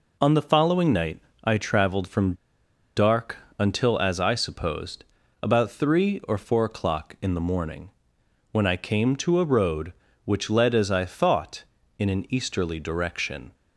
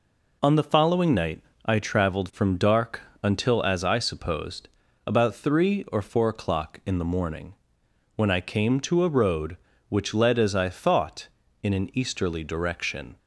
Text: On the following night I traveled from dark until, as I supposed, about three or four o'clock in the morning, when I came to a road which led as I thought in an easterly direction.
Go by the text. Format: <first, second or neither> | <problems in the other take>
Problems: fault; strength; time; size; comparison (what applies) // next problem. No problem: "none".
second | pauses between "night" and "I"; slight; at 1.1 s; 0.24 s long; slight in the second // pauses between "from" and "dark"; noticeable; at 2.3 s; 0.62 s long // pauses between "dark" and "until"; slight; at 3.3 s; 0.20 s long; slight in the second